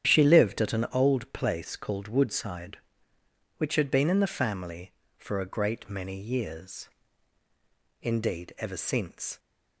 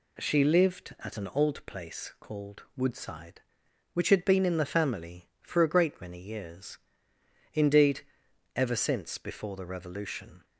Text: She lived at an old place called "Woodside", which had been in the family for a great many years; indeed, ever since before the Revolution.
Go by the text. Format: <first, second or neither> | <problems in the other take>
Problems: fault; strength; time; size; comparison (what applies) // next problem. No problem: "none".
second | starts louder than the rest; strong; until 1.1 s; 9 dB // stops before "before the Revolution"; at 9.3 s